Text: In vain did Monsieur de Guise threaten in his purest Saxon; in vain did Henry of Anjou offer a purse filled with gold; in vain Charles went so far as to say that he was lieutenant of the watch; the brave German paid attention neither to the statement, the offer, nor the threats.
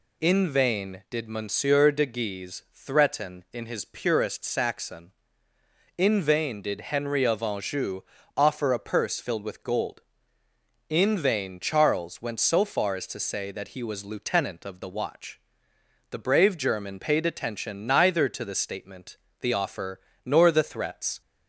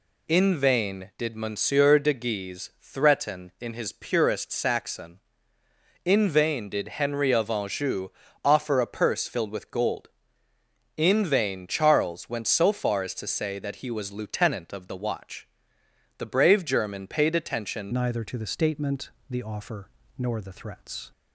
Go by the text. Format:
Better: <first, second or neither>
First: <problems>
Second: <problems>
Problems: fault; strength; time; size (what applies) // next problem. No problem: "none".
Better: first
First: pauses between "Anjou" and "offer"; slight; at 8.0 s; 0.36 s long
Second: pauses between "Anjou" and "offer"; slight; at 8.0 s; 0.36 s long // changes voice at "neither"; from 17.9 s on; 3.2 s long